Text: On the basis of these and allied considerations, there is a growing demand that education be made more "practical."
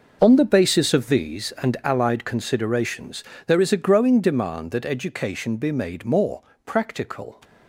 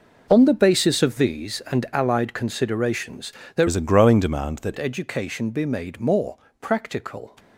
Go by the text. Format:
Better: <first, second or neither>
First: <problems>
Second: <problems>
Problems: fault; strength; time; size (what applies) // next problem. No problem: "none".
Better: first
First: pauses between "more" and "practical"; slight; at 6.4 s; 0.24 s long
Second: changes voice from "is" to "that"; from 3.6 to 4.7 s; 1.1 s long // pauses between "more" and "practical"; slight; at 6.3 s; 0.24 s long